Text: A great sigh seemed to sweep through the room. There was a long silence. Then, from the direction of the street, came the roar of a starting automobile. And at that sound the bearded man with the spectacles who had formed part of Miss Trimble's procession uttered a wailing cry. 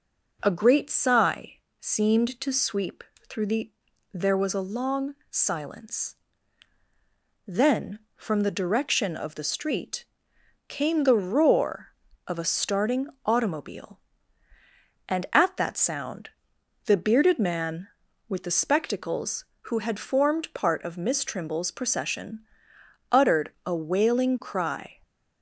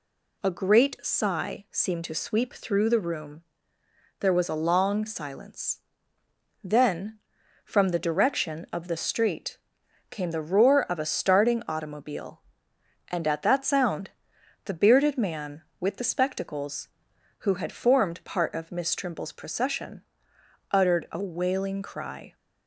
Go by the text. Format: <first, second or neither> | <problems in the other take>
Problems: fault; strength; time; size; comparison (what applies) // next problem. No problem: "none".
second | pauses between "sigh" and "seemed"; slight; at 1.5 s; 0.22 s long // pauses between "sweep" and "through"; slight; at 3.0 s; 0.24 s long // skips "room"; at 3.9 s // pauses between "long" and "silence"; slight; at 5.1 s; 0.16 s long // pauses between "starting" and "automobile"; slight; at 13.0 s; 0.18 s long // pauses between "sound" and "the"; noticeable; at 16.2 s; 0.56 s long; noticeable in the second // pauses between "procession" and "uttered"; noticeable; at 22.4 s; 0.68 s long; noticeable in the second